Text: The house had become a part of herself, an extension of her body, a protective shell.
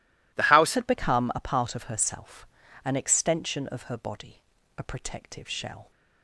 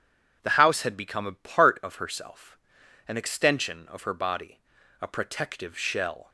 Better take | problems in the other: second | changes voice at "had"; from 0.7 s on; 5.2 s long

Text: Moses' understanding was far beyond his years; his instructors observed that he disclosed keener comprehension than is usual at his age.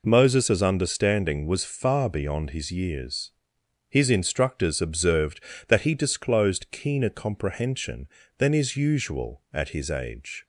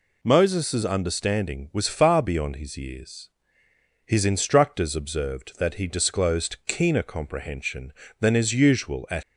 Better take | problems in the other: first | stops before "his age"; at 9.2 s

